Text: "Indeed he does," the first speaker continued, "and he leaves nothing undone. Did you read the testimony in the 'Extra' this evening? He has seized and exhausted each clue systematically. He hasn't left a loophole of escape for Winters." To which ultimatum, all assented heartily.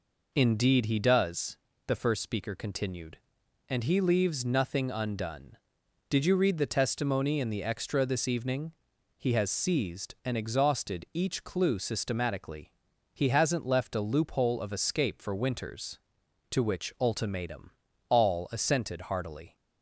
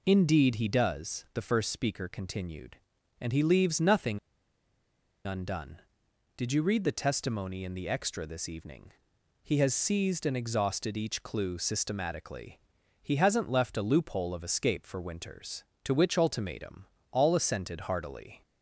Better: first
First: none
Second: pauses between "nothing" and "undone"; at 4.1 s; 1.0 s long

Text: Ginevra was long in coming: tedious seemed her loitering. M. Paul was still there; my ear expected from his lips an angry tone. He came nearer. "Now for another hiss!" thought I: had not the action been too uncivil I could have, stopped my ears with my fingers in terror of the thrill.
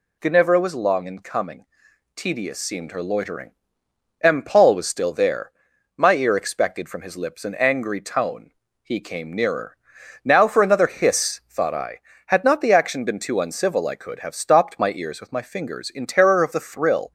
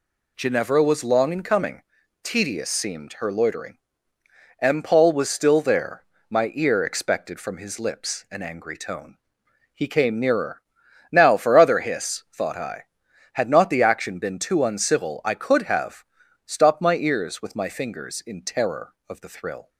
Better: first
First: none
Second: says "other" for "another"; at 11.5 s

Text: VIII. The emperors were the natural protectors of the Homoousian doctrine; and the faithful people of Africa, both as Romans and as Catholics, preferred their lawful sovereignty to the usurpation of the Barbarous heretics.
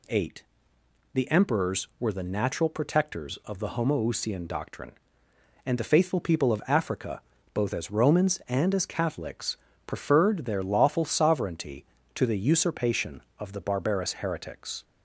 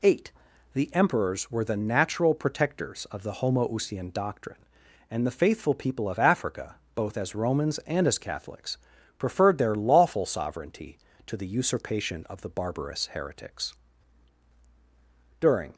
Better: first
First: none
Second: goes on to say "During"; slight; from 15.3 s on; 0.34 s long

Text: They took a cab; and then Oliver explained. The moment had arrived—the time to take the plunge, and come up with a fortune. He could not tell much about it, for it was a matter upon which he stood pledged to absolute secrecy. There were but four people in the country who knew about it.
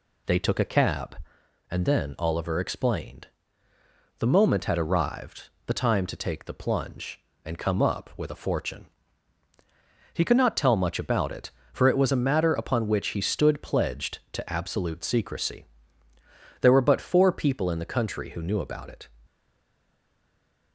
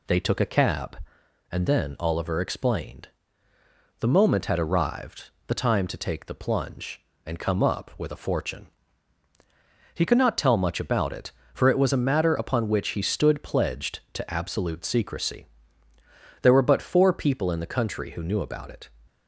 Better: second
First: stays silent after the last word; noticeable; from 19.2 s on; 1.5 s long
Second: none

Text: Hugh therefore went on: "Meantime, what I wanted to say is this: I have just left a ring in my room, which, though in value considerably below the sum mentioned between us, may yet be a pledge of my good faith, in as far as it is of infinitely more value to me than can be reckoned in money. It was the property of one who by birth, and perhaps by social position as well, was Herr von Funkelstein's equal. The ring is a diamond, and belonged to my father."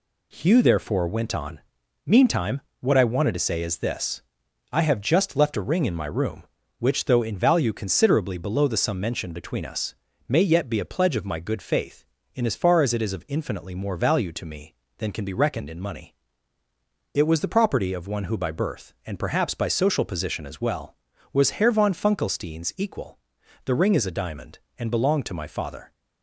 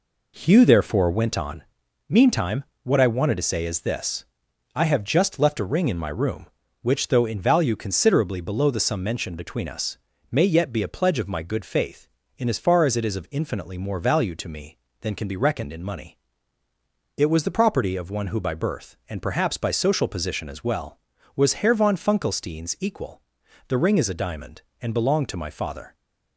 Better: first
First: none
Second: starts louder than the rest; until 1.4 s; 3.5 dB

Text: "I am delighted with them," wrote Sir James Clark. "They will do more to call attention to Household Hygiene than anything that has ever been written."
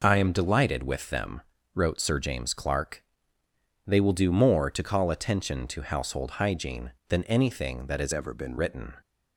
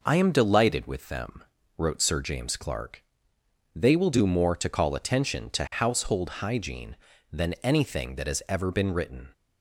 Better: second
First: changes voice from "ever" to "been"; from 8.1 to 8.5 s; 0.4 s long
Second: none

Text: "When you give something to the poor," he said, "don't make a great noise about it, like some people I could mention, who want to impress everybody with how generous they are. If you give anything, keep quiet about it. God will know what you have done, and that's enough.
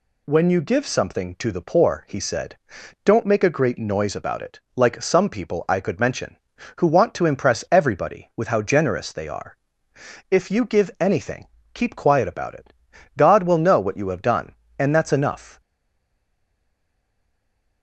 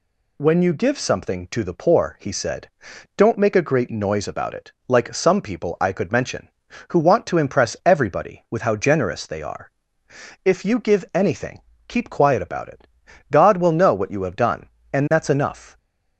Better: second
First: stays silent after the last word; from 15.6 s on; 2.2 s long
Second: none

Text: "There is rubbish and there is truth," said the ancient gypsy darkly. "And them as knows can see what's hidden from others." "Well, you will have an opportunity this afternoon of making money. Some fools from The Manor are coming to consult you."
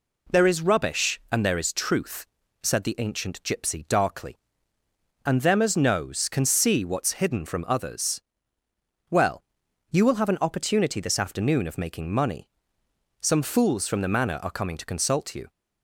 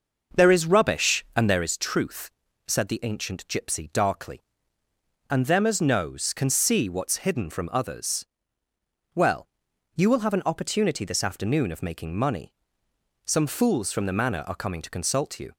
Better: first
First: none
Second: starts louder than the rest; noticeable; until 1.6 s; 6 dB

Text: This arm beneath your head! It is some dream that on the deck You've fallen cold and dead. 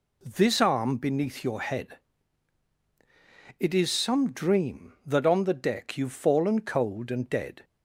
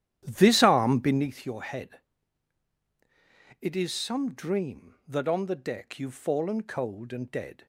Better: first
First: none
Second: starts louder than the rest; strong; until 1.3 s; 11 dB

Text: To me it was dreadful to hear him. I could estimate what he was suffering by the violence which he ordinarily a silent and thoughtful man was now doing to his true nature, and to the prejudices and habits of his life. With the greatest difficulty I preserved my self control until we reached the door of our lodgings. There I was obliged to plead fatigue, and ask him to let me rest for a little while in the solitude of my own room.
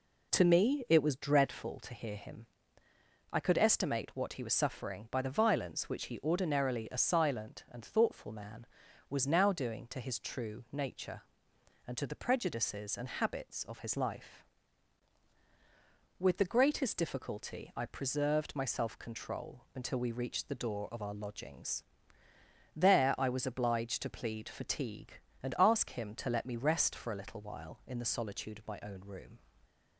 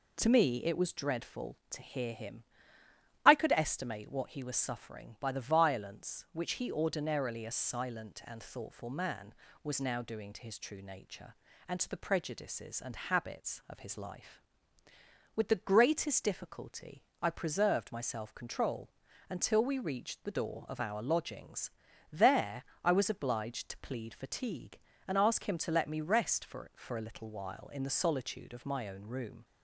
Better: first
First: none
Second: pauses between "difficulty" and "I"; slight; at 17.0 s; 0.18 s long // pauses between "control" and "until"; at 18.8 s; 0.40 s long // pauses between "There" and "I"; slight; at 22.6 s; 0.18 s long // says "for" twice; at 26.7 s

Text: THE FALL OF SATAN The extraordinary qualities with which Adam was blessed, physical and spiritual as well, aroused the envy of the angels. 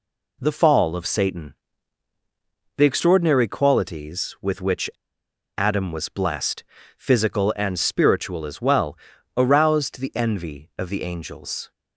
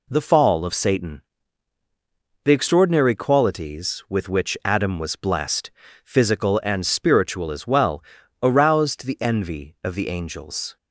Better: second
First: pauses between "SATAN" and "The"; at 1.5 s; 1.2 s long // pauses between "which" and "Adam"; noticeable; at 4.8 s; 0.68 s long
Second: pauses between "SATAN" and "The"; at 1.2 s; 1.2 s long

